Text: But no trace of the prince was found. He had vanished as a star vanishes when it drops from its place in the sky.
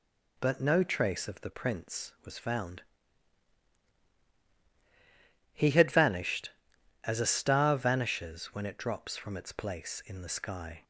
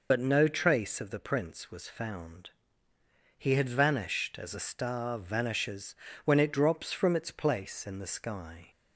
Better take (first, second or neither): first